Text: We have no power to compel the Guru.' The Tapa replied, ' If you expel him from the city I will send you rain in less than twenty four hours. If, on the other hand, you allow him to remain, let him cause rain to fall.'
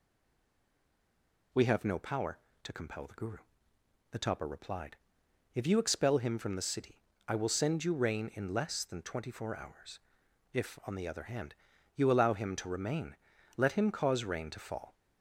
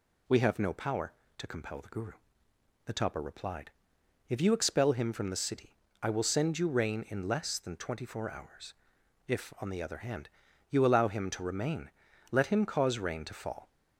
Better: second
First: stays silent before the first word; noticeable; until 1.5 s; 1.5 s long // pauses between "city" and "I"; slight; at 7.0 s; 0.26 s long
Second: pauses between "city" and "I"; slight; at 5.7 s; 0.26 s long

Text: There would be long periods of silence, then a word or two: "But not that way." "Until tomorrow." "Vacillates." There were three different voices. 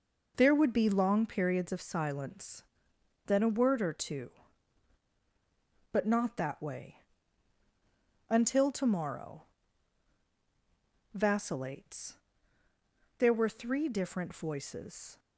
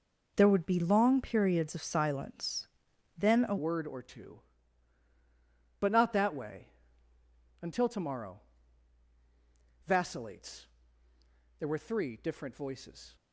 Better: first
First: none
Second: changes voice at "word"; from 3.5 s on; 9.6 s long

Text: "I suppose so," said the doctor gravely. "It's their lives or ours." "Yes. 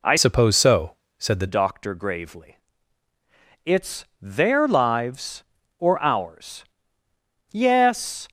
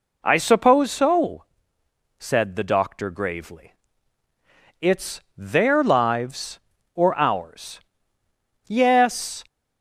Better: second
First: changes voice from "suppose" to "the"; from 0.1 to 1.4 s; 1.3 s long // pauses between "It's" and "their"; slight; at 4.0 s; 0.16 s long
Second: pauses between "It's" and "their"; slight; at 5.1 s; 0.16 s long

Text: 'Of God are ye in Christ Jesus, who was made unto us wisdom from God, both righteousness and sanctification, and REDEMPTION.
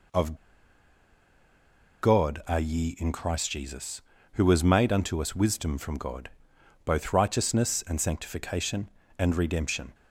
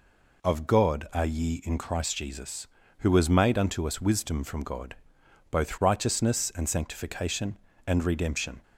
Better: second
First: pauses between "Of" and "God"; strong; at 0.3 s; 1.6 s long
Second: none

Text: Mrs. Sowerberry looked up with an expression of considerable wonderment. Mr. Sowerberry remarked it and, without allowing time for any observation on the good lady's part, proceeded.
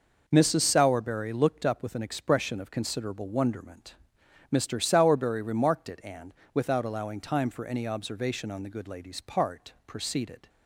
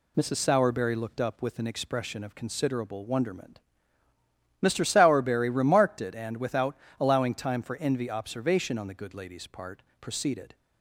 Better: first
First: none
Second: pauses between "without" and "allowing"; slight; at 6.7 s; 0.24 s long // says "envy" for "any"; at 7.7 s

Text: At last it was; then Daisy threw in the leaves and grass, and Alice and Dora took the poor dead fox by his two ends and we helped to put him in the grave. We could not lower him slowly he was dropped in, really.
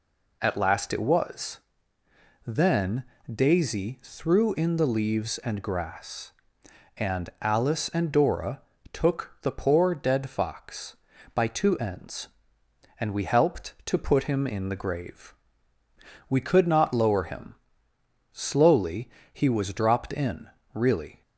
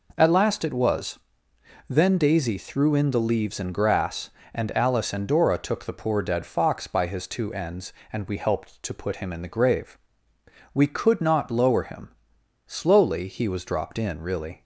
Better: second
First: pauses between "then" and "Daisy"; slight; at 3.0 s; 0.30 s long // pauses between "Dora" and "took"; slight; at 8.6 s; 0.32 s long // skips "his"; at 11.4 s // pauses between "him" and "slowly"; noticeable; at 17.5 s; 0.82 s long // pauses between "slowly" and "he"; slight; at 19.0 s; 0.22 s long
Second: pauses between "him" and "slowly"; noticeable; at 12.0 s; 0.58 s long

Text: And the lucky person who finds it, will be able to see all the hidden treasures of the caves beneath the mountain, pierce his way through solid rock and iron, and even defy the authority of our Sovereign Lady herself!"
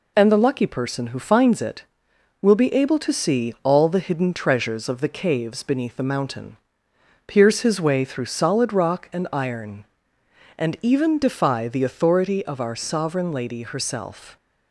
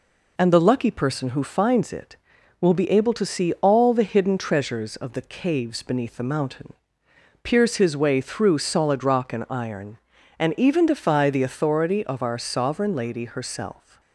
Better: neither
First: none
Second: none

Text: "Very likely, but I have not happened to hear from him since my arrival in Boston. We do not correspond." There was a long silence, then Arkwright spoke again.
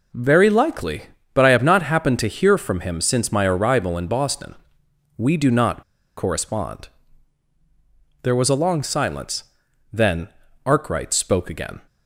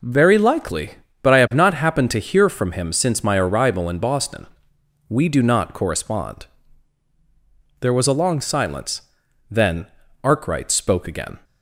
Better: second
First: pauses between "not" and "correspond"; slight; at 5.8 s; 0.35 s long // pauses between "then" and "Arkwright"; at 10.2 s; 0.38 s long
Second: pauses between "then" and "Arkwright"; at 9.8 s; 0.38 s long

